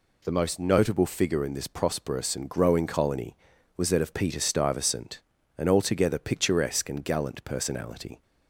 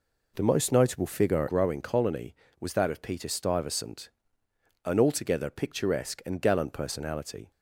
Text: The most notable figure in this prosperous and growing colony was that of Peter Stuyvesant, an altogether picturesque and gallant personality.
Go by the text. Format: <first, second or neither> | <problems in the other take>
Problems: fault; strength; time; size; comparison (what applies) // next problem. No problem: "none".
first | skips "in this prosperous and"; at 1.4 s